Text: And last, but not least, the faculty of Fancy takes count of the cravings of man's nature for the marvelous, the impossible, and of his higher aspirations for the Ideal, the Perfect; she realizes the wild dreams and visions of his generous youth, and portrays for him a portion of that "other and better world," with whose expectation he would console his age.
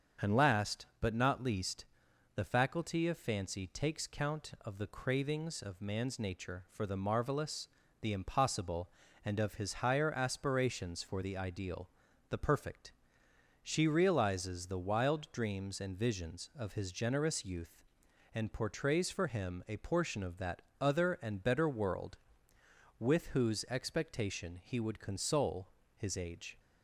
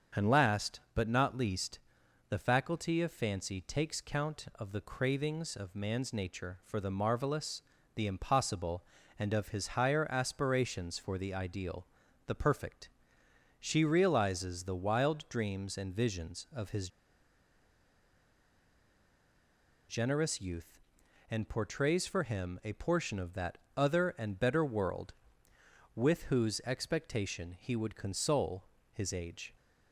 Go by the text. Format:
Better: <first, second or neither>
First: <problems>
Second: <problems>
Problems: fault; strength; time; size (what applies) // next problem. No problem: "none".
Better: first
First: starts louder than the rest; strong; until 1.3 s; 7.5 dB // pauses between "that" and "other"; slight; at 20.6 s; 0.18 s long // pauses between "console" and "his"; slight; at 25.6 s; 0.26 s long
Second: starts louder than the rest; strong; until 1.3 s; 7.5 dB // pauses between "his" and "generous"; strong; at 16.8 s; 3.0 s long // pauses between "that" and "other"; slight; at 23.5 s; 0.18 s long // pauses between "console" and "his"; slight; at 28.6 s; 0.26 s long